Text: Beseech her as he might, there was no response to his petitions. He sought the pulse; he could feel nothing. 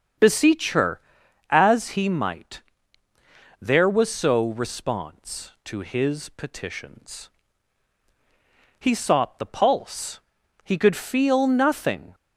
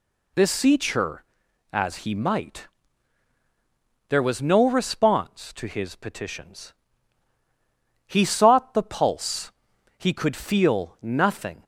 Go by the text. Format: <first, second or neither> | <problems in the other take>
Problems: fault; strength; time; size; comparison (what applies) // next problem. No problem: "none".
second | starts louder than the rest; until 1.6 s; 7 dB // says "so" for "no"; at 4.1 s